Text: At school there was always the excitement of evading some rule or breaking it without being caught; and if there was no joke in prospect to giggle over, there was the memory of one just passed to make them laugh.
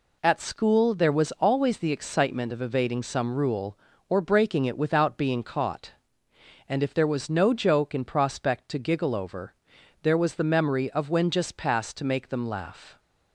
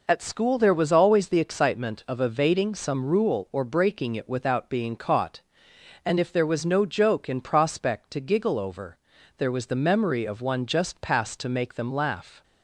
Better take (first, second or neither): second